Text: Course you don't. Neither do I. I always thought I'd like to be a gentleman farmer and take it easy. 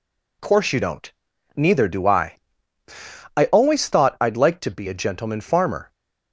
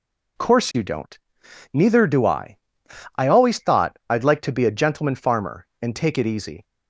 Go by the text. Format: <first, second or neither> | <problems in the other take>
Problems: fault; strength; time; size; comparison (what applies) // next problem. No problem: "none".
second | stops before "and take it easy"; at 5.9 s